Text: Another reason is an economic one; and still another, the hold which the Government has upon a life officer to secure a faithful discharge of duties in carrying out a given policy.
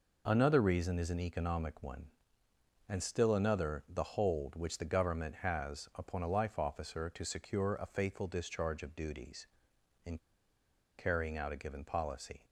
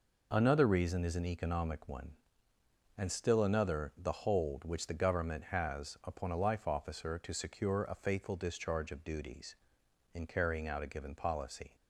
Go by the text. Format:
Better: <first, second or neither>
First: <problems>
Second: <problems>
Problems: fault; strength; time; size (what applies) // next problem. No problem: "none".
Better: second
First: pauses between "in" and "carrying"; noticeable; at 10.1 s; 0.80 s long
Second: none